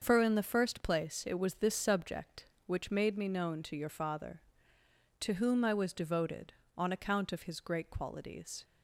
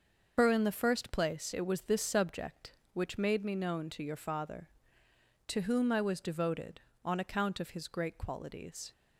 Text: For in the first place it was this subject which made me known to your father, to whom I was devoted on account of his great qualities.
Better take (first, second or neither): first